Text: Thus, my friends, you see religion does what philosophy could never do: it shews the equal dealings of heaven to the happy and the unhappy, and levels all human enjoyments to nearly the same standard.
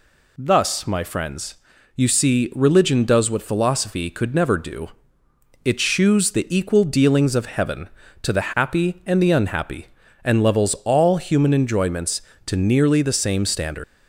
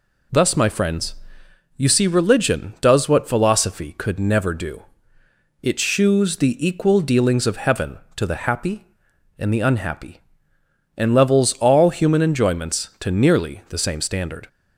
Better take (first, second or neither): second